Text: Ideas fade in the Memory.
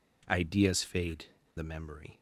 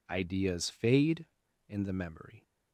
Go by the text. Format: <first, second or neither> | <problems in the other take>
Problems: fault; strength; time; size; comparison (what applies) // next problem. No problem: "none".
second | skips "in"; at 1.4 s